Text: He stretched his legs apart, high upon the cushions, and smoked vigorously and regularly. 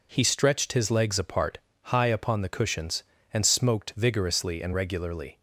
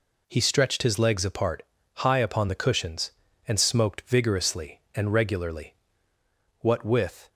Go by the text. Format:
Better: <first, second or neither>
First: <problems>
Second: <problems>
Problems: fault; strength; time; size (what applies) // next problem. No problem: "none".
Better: first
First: none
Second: goes on to say "What with"; noticeable; from 6.5 s on; 0.68 s long